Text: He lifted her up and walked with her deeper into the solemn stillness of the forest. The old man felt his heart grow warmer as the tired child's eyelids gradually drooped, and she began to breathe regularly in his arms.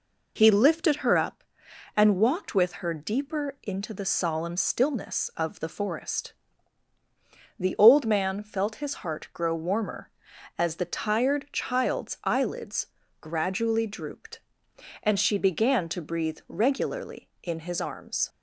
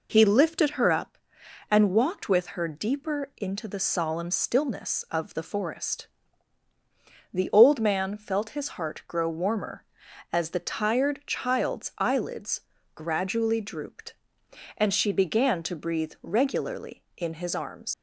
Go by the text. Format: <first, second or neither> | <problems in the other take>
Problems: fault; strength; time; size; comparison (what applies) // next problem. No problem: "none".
first | pauses between "eyelids" and "gradually"; at 12.5 s; 0.38 s long; also in the first // leaves "arms" unfinished; at 17.9 s; 90 ms